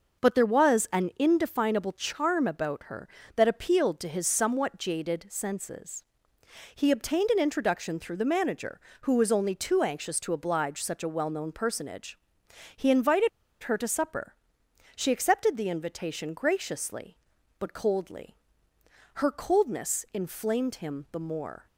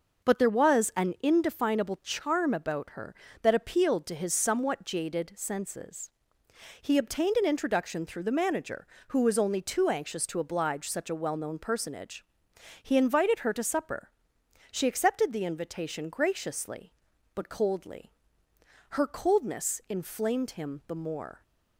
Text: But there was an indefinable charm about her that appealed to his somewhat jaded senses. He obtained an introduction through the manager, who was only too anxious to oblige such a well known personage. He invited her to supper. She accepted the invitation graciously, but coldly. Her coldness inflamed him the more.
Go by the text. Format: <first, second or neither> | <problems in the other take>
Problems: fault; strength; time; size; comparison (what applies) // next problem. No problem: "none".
second | pauses between "invited" and "her"; slight; at 13.2 s; 0.33 s long